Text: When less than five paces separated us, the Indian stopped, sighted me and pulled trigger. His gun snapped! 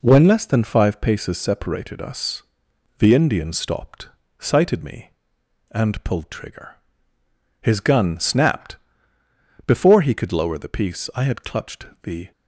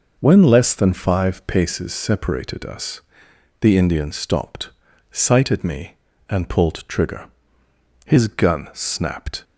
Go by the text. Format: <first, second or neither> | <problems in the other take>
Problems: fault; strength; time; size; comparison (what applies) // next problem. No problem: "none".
second | goes on to say "Before he could lower the piece I had clutched the"; strong; from 9.6 s on; 2.6 s long